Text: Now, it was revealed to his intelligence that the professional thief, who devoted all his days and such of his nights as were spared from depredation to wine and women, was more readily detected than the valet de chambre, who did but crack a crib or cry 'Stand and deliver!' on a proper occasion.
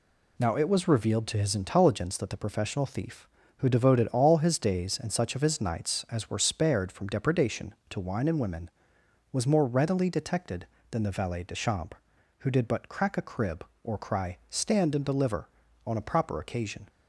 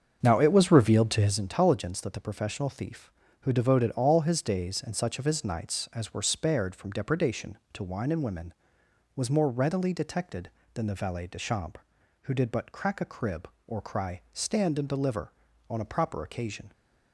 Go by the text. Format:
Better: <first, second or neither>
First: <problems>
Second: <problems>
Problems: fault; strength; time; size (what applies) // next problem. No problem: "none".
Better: first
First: none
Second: starts louder than the rest; until 1.4 s; 7 dB